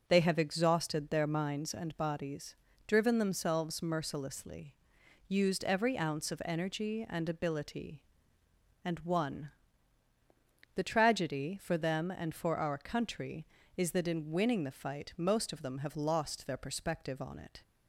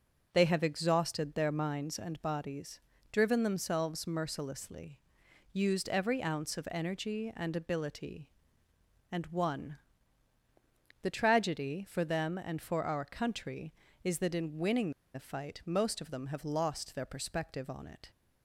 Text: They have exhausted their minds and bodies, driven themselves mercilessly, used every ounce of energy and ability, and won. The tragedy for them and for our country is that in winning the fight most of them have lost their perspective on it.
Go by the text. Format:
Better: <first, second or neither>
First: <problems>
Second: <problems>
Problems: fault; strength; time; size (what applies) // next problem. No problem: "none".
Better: first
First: starts louder than the rest; until 1.0 s; 6.5 dB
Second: starts louder than the rest; until 1.3 s; 6.5 dB // pauses between "winning" and "the"; slight; at 14.9 s; 0.23 s long